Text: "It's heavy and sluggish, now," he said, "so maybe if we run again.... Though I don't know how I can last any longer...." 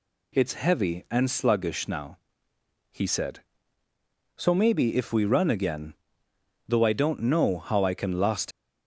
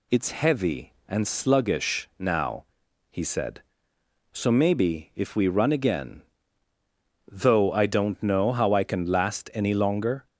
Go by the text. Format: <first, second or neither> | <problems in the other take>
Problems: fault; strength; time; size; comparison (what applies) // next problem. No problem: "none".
second | stops before "any longer"; at 8.5 s